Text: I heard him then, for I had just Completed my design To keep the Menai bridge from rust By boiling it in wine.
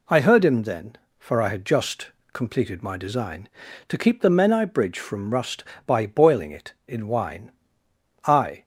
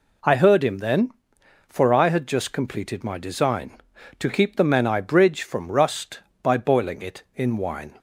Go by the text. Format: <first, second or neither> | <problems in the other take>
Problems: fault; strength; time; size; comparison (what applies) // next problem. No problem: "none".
second | pauses between "just" and "Completed"; slight; at 2.1 s; 0.24 s long // goes on to say "I"; slight; from 8.2 s on; 0.38 s long